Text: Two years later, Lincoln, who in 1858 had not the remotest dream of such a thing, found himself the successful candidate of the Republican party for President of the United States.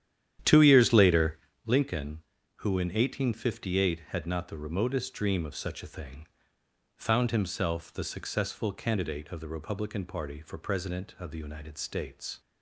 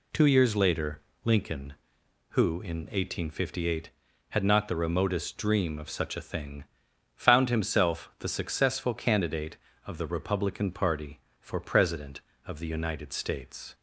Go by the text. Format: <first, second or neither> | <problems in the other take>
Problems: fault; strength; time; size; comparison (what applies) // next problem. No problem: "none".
second | starts louder than the rest; strong; until 1.7 s; 10.5 dB